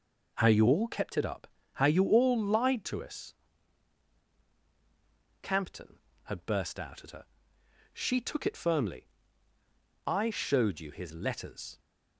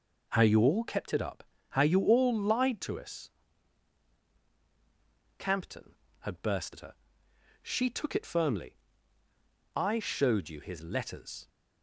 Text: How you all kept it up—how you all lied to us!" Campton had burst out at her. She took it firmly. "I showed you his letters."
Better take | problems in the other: first | skips "out"; at 6.7 s

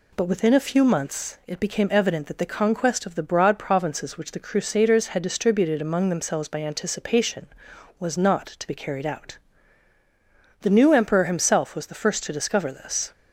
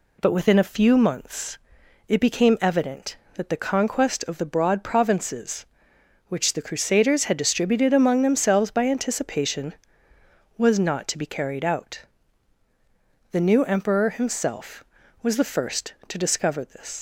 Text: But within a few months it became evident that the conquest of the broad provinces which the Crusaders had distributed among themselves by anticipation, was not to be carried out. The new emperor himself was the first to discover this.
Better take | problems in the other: first | pauses between "months" and "it"; noticeable; at 1.5 s; 0.52 s long // leaves "this" unfinished; at 16.9 s; 115 ms

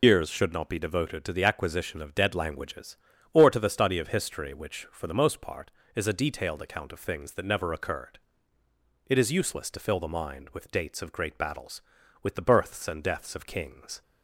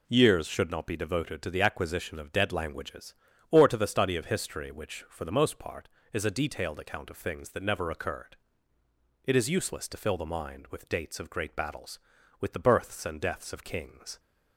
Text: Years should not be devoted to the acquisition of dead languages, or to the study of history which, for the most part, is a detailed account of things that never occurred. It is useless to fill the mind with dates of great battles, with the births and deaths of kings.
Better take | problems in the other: second | loses the start of "Years"; at 0.0 s; 135 ms

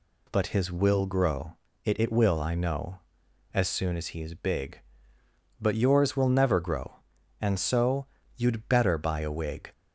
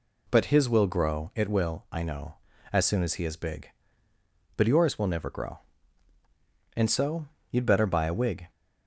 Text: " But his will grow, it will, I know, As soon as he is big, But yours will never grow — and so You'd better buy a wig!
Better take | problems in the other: second | says "it" twice; at 1.9 s // pauses between "so" and "You'd"; slight; at 8.0 s; 0.28 s long; slight in the second

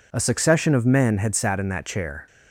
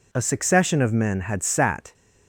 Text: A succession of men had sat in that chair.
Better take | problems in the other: first | stops before "in that chair"; at 1.9 s

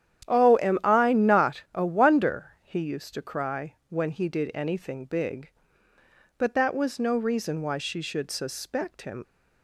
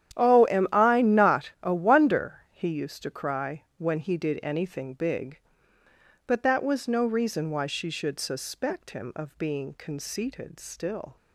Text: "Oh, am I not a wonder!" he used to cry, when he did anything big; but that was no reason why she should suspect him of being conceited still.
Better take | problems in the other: second | starts louder than the rest; strong; until 1.3 s; 10.5 dB; strong in the second // stops before "of being conceited still"; at 9.2 s

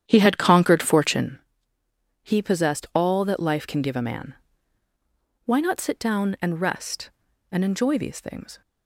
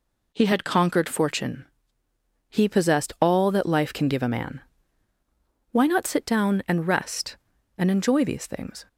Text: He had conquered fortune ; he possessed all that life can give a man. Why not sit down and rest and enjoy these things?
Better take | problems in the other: second | starts louder than the rest; strong; until 1.4 s; 9.5 dB

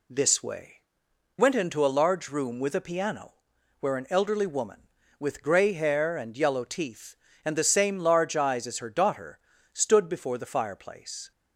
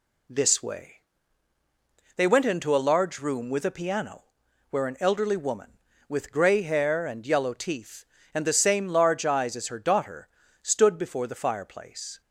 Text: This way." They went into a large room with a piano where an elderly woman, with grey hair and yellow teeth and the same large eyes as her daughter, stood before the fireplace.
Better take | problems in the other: second | skips "They"; at 1.0 s // pauses between "piano" and "where"; noticeable; at 3.3 s; 0.46 s long; noticeable in the second

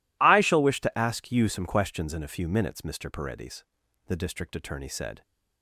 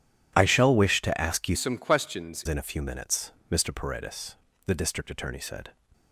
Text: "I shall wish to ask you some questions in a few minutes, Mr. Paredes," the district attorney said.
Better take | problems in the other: first | changes voice from "some" to "questions"; from 1.5 to 2.4 s; 0.9 s long

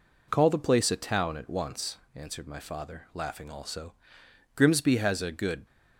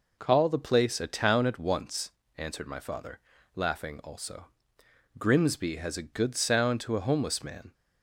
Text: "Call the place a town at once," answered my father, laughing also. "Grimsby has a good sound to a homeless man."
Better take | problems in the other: second | stops before "sound to a homeless man"; at 5.6 s

